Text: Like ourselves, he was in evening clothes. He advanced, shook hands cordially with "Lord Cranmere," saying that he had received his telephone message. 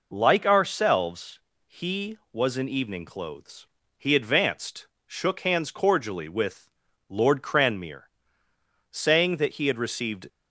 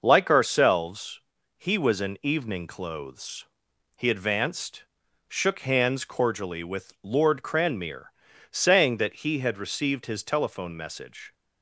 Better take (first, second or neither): second